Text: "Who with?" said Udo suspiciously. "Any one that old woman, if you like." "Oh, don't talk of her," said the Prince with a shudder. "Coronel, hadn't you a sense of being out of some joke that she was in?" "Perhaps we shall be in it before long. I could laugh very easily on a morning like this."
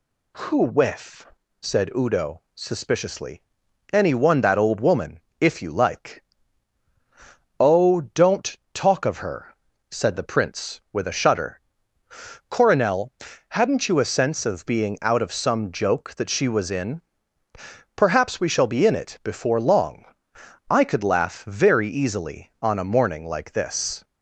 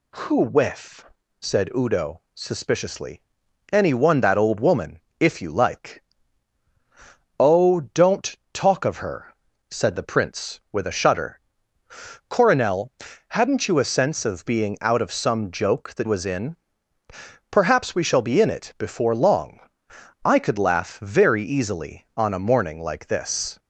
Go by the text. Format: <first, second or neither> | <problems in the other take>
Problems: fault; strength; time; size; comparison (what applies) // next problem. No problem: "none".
first | pauses between "don't" and "talk"; slight; at 8.3 s; 0.16 s long; slight in the first // skips "she"; at 16.0 s